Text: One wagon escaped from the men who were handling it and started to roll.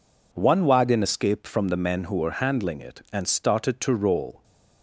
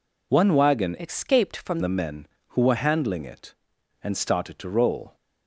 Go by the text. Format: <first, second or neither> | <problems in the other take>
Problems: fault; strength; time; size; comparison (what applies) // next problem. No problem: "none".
first | changes voice from "escaped" to "from"; from 0.9 to 1.7 s; 0.8 s long